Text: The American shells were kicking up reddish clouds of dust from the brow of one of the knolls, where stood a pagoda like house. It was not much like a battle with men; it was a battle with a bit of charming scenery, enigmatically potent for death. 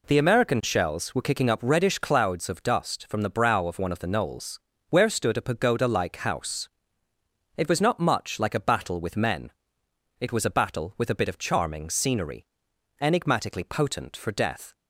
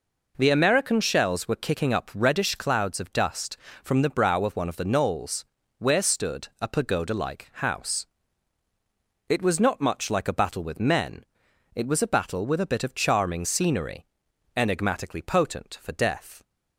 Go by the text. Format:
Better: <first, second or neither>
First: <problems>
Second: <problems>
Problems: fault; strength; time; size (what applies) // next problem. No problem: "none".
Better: neither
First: none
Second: none